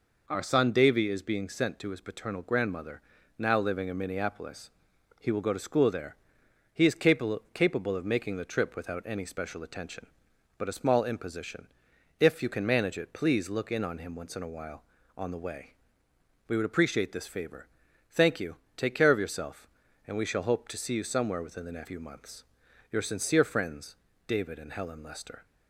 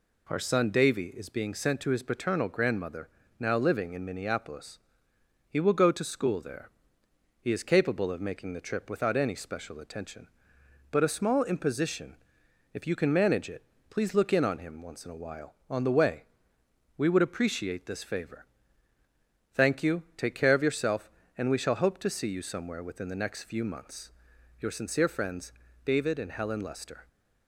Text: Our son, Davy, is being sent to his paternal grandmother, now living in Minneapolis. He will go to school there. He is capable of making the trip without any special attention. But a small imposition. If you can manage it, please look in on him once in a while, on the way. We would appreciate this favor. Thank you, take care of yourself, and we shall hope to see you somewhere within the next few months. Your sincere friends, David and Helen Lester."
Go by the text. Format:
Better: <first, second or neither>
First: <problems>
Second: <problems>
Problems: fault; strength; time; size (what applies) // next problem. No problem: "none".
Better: second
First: says "capable" twice; at 7.5 s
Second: none